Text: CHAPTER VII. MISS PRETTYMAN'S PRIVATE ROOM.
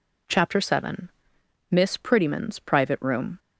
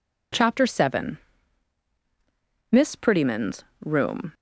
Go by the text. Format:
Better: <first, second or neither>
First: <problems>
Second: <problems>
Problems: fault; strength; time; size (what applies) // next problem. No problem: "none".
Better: first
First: none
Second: skips "PRIVATE"; at 3.7 s